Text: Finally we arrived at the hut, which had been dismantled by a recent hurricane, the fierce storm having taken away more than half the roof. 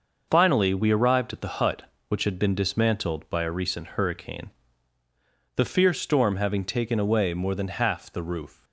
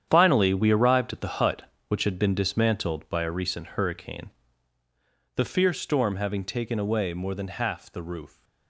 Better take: first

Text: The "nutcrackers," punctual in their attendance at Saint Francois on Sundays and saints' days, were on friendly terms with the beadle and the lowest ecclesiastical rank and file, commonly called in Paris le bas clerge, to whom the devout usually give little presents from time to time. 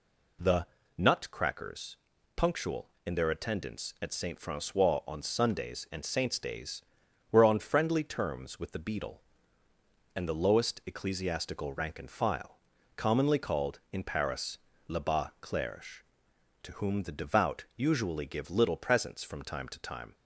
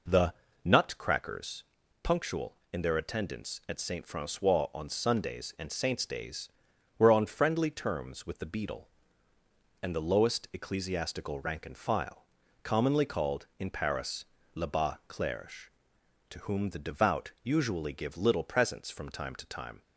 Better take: first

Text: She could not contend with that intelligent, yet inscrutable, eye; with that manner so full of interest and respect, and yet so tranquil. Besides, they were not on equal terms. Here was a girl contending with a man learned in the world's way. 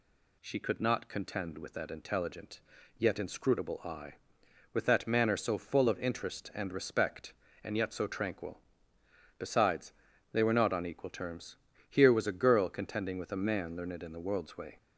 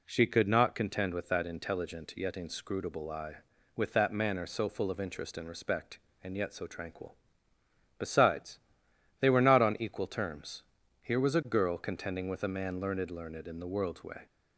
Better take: first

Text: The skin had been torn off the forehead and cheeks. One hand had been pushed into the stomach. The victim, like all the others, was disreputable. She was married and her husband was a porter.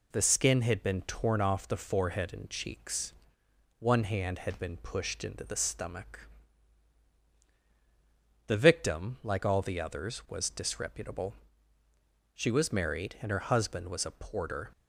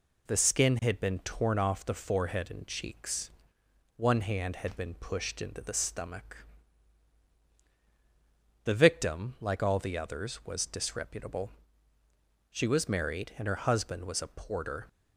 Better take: neither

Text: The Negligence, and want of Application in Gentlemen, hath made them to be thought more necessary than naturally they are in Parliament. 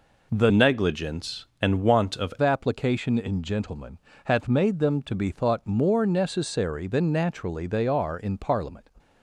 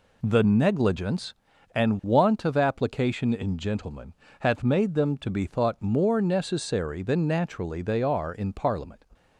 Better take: second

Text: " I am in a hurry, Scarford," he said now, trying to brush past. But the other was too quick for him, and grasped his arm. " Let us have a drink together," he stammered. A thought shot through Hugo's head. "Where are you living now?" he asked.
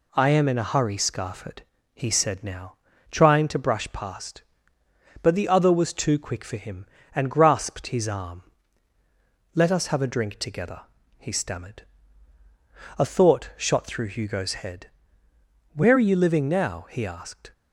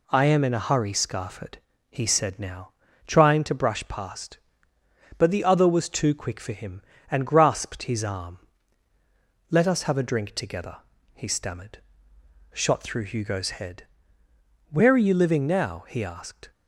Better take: first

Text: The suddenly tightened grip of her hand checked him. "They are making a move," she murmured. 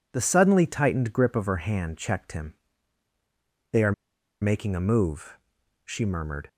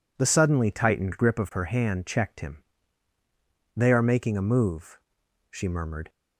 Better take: second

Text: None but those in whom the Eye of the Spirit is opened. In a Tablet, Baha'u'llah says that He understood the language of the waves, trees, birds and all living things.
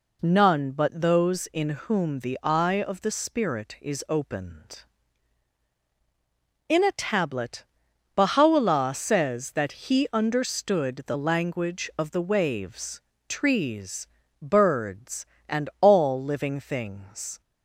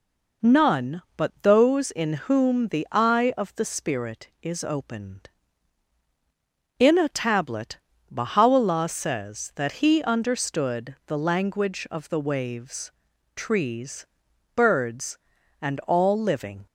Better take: first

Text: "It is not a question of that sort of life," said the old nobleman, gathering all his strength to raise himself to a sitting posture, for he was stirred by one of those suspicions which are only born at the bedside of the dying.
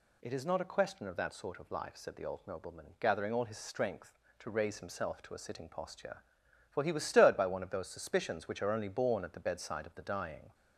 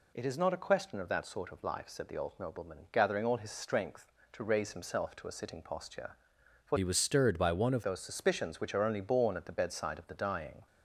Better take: first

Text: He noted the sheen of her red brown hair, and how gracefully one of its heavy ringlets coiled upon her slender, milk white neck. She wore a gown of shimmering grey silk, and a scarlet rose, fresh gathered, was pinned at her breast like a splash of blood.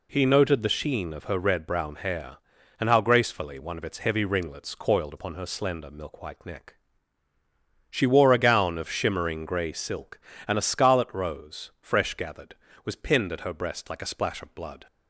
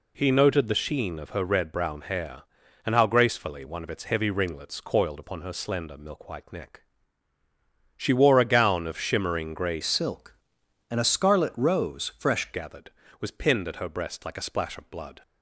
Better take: first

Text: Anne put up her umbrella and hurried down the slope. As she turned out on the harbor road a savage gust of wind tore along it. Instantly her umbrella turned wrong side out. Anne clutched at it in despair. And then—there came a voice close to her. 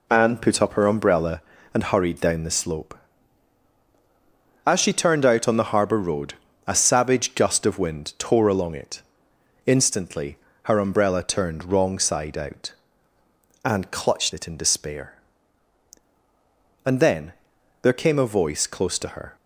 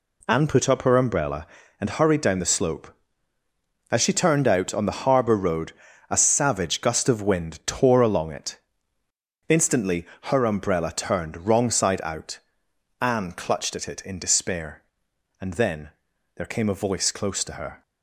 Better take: second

